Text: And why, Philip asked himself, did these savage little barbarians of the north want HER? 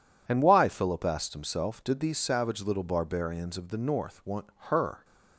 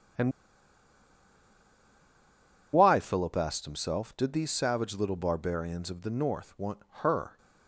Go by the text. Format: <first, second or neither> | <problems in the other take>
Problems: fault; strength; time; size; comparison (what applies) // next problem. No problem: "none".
first | pauses between "And" and "why"; strong; at 0.3 s; 2.4 s long // pauses between "want" and "HER"; slight; at 6.7 s; 0.22 s long; slight in the first